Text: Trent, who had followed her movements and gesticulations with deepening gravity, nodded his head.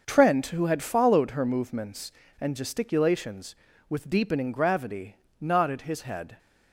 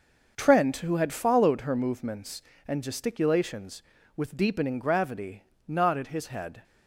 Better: neither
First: starts louder than the rest; until 1.0 s; 6 dB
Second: starts louder than the rest; noticeable; until 1.3 s; 6 dB

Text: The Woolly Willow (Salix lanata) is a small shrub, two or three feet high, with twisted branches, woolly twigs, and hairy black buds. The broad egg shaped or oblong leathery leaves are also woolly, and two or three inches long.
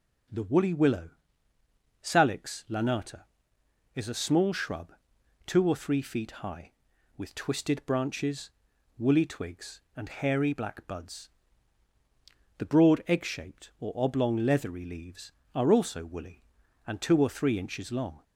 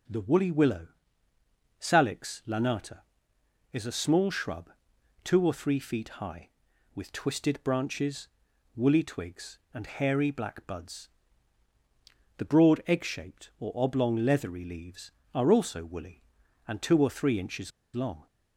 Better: first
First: none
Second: pauses between "inches" and "long"; slight; at 17.7 s; 0.23 s long

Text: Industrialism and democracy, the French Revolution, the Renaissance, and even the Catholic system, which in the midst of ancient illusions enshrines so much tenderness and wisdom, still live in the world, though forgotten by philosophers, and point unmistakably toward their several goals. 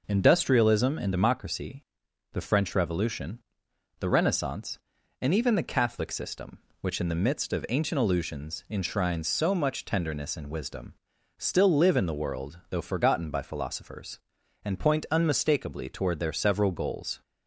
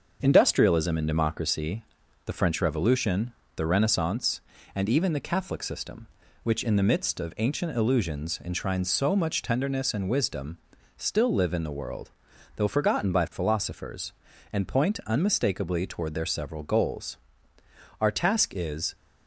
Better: first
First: none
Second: starts louder than the rest; until 1.2 s; 6.5 dB // goes on to say "Our task is"; noticeable; from 18.0 s on; 0.94 s long

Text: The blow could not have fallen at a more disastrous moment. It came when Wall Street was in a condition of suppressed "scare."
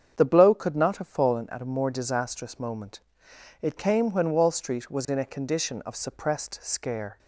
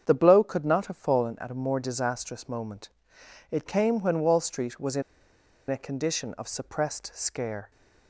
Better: first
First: starts louder than the rest; strong; until 1.1 s; 7.5 dB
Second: starts louder than the rest; strong; until 1.0 s; 7.5 dB // pauses between "in" and "a"; noticeable; at 5.0 s; 0.67 s long

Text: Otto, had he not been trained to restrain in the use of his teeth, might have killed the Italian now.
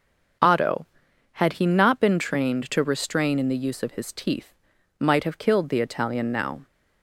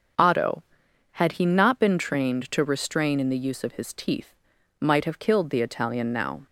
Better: neither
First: starts louder than the rest; until 1.8 s; 6.5 dB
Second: starts louder than the rest; until 1.6 s; 6.5 dB

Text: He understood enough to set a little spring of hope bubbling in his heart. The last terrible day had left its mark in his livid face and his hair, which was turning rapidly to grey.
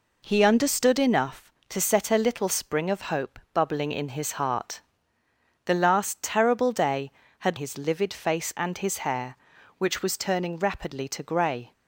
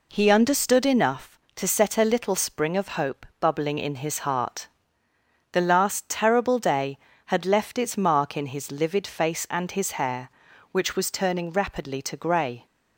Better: second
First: skips "left its mark in"; at 7.5 s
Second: none

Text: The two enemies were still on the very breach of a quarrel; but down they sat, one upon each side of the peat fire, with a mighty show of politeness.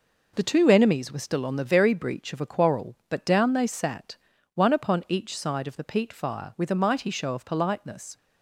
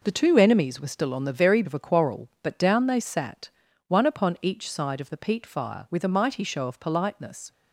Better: first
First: none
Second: skips "breach"; at 1.6 s

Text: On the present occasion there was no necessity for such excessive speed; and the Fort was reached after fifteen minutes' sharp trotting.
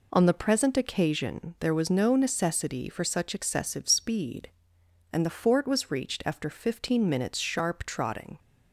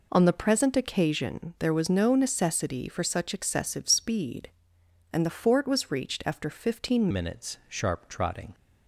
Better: first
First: none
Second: changes voice at "minutes"; from 7.1 s on; 1.4 s long

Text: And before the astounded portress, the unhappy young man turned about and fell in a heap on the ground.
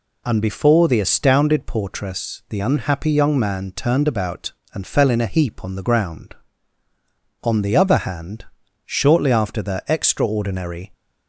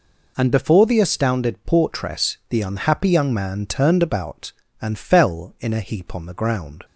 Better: second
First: goes on to say "On the other hand shortly after the extraordinary"; strong; from 7.4 s on; 3.5 s long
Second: none

